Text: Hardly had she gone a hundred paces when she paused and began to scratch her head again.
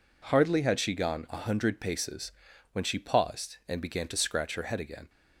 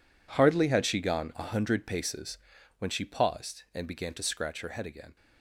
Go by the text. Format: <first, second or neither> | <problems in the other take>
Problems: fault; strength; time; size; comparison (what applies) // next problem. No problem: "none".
first | gets quieter; strong; throughout; 14.5 dB // pauses between "paces" and "when"; at 2.3 s; 0.40 s long; also in the first